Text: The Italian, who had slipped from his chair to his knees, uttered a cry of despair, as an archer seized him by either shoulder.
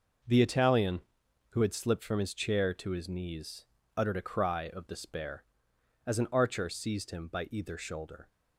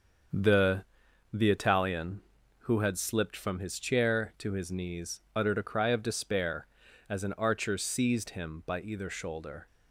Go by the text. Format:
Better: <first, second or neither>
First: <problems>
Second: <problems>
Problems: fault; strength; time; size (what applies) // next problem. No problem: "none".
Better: first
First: none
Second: starts louder than the rest; until 1.7 s; 7 dB // says "The" twice; at 1.3 s